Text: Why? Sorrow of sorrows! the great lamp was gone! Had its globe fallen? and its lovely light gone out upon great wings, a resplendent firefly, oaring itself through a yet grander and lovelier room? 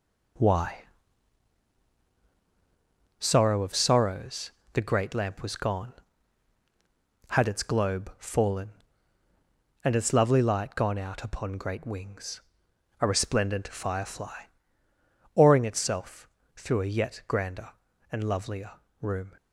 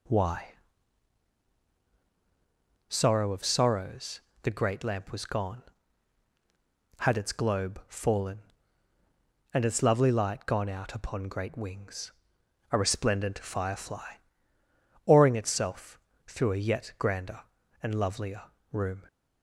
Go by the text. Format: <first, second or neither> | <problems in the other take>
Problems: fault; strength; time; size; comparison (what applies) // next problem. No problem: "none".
second | gets quieter; throughout; 6.5 dB // pauses between "itself" and "through"; slight; at 16.2 s; 0.28 s long; slight in the second // pauses between "lovelier" and "room"; slight; at 18.7 s; 0.28 s long; slight in the second